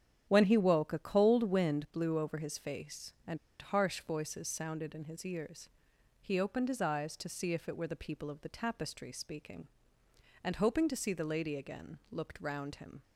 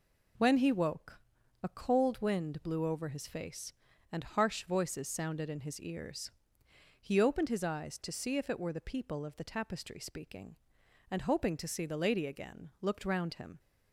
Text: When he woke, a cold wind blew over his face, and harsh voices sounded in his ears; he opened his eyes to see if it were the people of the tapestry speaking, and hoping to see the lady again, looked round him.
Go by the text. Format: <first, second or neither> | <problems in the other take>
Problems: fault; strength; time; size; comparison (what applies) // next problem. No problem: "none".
second | starts louder than the rest; strong; until 1.2 s; 9 dB // pauses between "and" and "harsh"; slight; at 3.3 s; 0.23 s long